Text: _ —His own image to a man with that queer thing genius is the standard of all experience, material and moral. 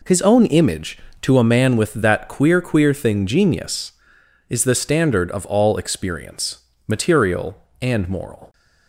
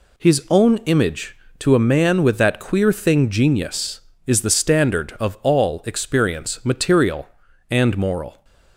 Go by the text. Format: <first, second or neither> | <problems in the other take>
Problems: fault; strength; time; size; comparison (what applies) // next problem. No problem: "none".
second | says "queer" twice; at 2.6 s